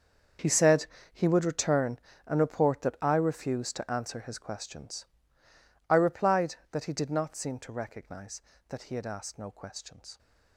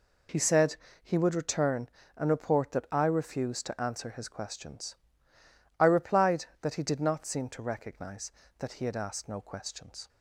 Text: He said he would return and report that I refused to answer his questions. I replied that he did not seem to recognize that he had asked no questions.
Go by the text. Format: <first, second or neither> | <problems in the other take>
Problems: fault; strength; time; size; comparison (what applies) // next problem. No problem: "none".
second | gets quieter; strong; throughout; 15 dB // pauses between "said" and "he"; slight; at 0.8 s; 0.26 s long; slight in the second